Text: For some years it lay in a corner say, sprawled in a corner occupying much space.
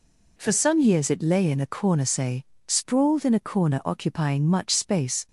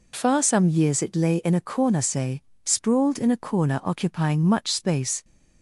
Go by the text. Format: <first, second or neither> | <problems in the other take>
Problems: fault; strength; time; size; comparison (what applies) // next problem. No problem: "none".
first | says "Far" for "For"; at 0.1 s